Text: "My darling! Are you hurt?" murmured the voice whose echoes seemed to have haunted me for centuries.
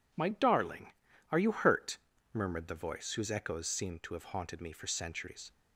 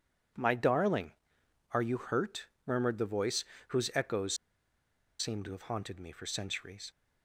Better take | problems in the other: first | pauses between "voice" and "whose"; slight; at 3.4 s; 0.24 s long // pauses between "echoes" and "seemed"; noticeable; at 4.3 s; 0.84 s long

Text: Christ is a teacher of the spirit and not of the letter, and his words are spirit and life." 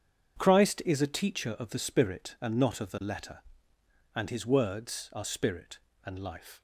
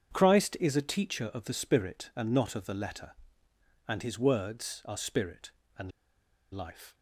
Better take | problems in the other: first | starts louder than the rest; strong; until 1.1 s; 8 dB; strong in the first // pauses between "and" and "life"; noticeable; at 5.8 s; 0.62 s long

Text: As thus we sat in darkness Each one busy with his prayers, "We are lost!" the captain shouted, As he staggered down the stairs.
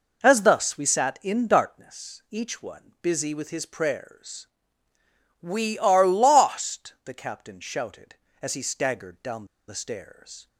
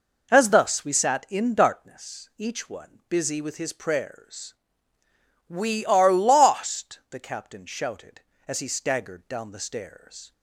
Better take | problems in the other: second | pauses between "down" and "the"; slight; at 9.4 s; 0.23 s long

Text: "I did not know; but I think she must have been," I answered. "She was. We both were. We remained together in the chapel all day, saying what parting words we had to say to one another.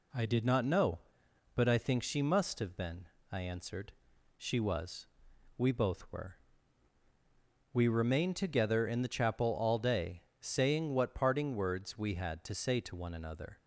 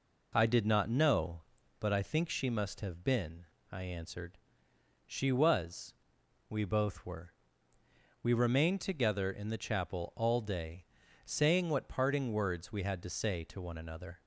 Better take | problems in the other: neither | none

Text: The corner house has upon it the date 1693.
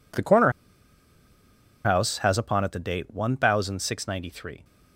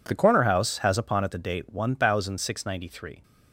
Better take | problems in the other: second | pauses between "corner" and "house"; strong; at 0.5 s; 1.3 s long

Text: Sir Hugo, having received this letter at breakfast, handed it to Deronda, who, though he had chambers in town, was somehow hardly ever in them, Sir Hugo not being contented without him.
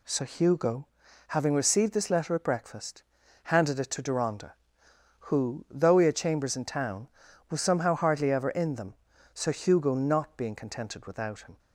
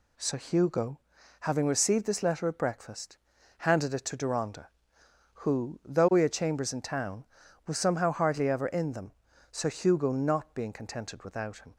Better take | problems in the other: neither | none

